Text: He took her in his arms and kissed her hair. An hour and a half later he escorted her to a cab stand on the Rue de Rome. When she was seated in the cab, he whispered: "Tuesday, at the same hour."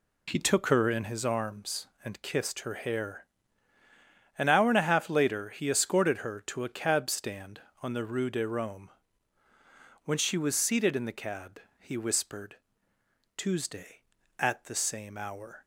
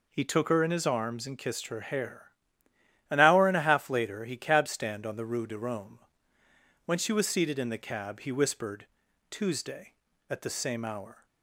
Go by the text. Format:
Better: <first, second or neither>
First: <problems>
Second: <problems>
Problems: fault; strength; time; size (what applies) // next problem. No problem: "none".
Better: first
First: none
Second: skips "escorted her to a"; at 4.3 s